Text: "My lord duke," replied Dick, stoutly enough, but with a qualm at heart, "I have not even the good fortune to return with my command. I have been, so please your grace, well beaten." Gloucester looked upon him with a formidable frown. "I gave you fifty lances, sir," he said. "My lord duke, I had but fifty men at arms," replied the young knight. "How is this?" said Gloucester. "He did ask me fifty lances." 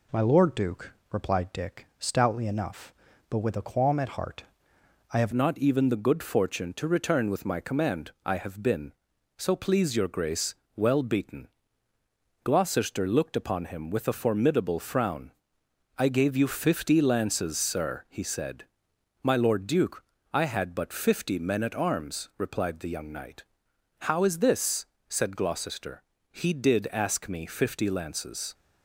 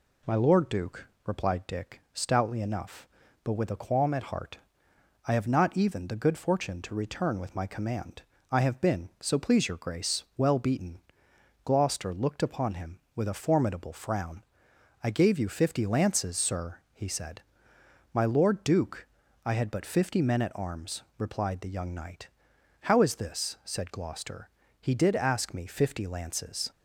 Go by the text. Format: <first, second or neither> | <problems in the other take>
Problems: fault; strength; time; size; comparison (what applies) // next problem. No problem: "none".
second | changes voice at "not"; from 5.3 s on; 23.2 s long